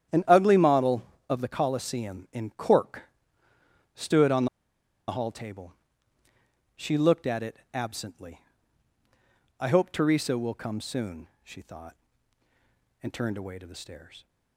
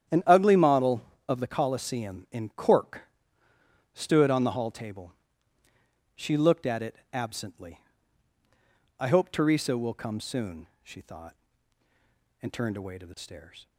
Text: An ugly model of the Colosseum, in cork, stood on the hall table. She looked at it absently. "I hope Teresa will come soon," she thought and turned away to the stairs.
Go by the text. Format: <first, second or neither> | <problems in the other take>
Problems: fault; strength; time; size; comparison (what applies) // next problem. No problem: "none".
second | starts louder than the rest; strong; until 1.3 s; 10 dB; strong in the second // pauses between "on" and "the"; noticeable; at 4.4 s; 0.61 s long // pauses between "it" and "absently"; slight; at 7.5 s; 0.16 s long; slight in the second